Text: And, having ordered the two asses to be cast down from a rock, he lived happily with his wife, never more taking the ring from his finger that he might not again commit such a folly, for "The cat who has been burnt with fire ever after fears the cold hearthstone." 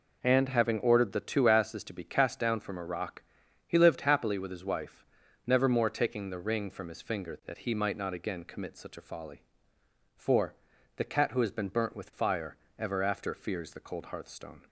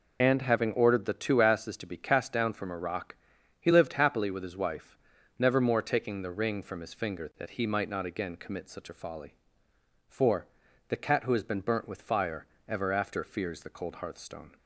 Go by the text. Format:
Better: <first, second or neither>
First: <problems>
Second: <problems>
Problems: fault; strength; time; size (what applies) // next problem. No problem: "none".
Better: first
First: pauses between "for" and "The"; at 10.5 s; 0.40 s long // pauses between "fire" and "ever"; slight; at 12.5 s; 0.22 s long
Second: loses the start of "And"; at 0.2 s; 50 ms // pauses between "for" and "The"; at 10.4 s; 0.40 s long // pauses between "fire" and "ever"; slight; at 12.4 s; 0.22 s long